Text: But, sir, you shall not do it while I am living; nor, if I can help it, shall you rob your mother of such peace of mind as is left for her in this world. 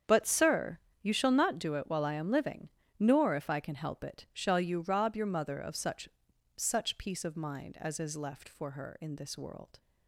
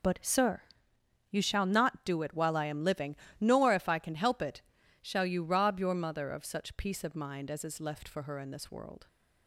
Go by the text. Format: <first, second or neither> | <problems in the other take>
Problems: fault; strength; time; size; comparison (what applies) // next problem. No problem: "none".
second | starts louder than the rest; strong; until 1.2 s; 8 dB // says "such" twice; at 6.5 s